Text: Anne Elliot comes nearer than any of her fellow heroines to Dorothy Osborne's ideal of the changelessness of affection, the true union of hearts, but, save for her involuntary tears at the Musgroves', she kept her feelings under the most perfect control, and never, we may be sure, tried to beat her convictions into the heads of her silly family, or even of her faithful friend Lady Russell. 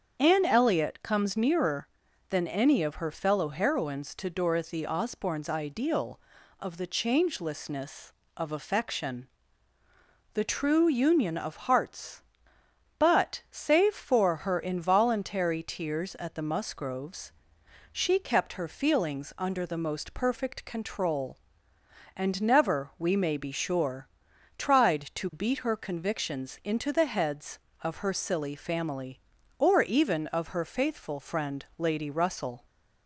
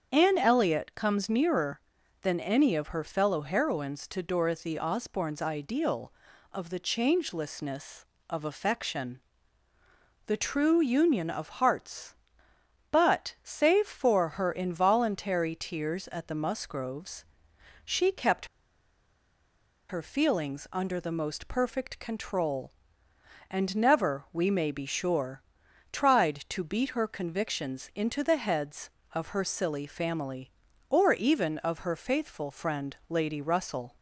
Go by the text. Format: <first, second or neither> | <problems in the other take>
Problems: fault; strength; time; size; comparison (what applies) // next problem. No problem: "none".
first | starts louder than the rest; until 1.1 s; 7 dB; also in the first // pauses between "kept" and "her"; strong; at 18.4 s; 1.4 s long